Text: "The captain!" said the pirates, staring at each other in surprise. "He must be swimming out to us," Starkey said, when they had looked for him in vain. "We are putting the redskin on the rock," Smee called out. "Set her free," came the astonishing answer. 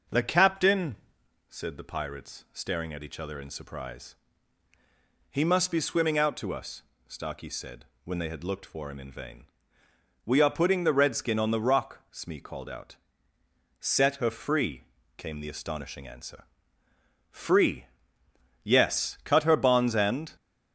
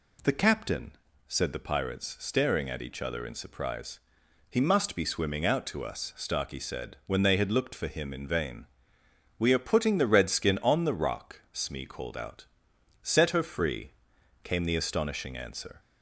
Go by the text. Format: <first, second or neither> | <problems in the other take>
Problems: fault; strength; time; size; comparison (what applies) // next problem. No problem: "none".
second | goes on to say "Free Yes cut her bonds and"; strong; from 17.2 s on; 3.0 s long